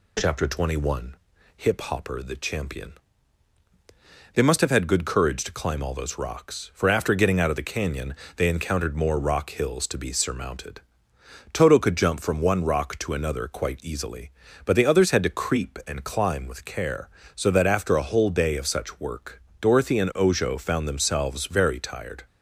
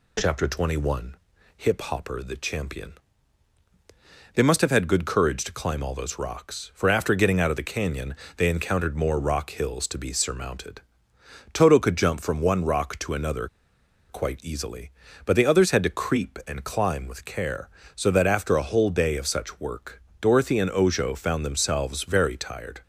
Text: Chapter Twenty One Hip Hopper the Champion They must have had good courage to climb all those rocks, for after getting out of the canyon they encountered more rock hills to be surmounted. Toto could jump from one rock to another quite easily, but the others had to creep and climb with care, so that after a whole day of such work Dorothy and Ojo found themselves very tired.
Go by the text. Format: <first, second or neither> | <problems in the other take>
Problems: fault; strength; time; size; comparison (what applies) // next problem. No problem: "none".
first | pauses between "One" and "Hip"; at 1.1 s; 0.44 s long; also in the first // pauses between "Champion" and "They"; strong; at 2.9 s; 1.4 s long; strong in the first // pauses between "canyon" and "they"; slight; at 8.1 s; 0.20 s long; slight in the first // pauses between "another" and "quite"; noticeable; at 13.4 s; 0.62 s long // pauses between "work" and "Dorothy"; slight; at 19.9 s; 0.20 s long; slight in the first